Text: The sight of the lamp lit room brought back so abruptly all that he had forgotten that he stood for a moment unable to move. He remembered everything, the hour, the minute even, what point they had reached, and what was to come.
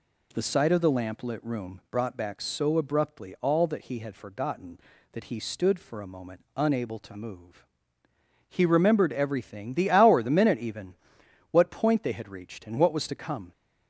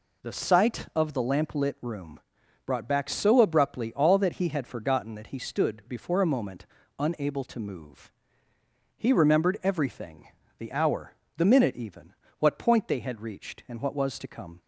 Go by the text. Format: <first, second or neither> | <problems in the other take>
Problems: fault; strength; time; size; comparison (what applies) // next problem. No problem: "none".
first | pauses between "room" and "brought"; noticeable; at 2.2 s; 0.46 s long // says "before" for "for"; at 5.8 s // pauses between "moment" and "unable"; slight; at 6.6 s; 0.32 s long